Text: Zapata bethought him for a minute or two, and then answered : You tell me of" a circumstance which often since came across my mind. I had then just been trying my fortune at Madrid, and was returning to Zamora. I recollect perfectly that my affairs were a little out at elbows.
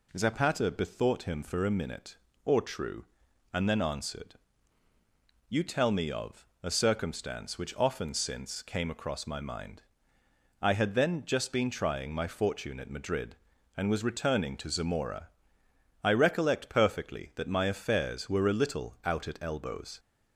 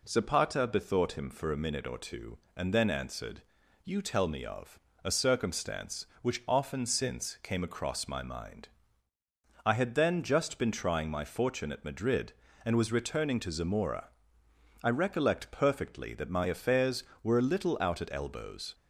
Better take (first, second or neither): second